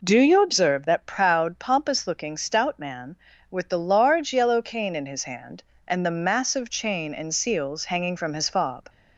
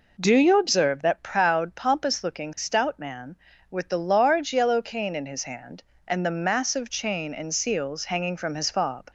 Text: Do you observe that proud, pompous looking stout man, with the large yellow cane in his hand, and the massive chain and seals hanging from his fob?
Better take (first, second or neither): neither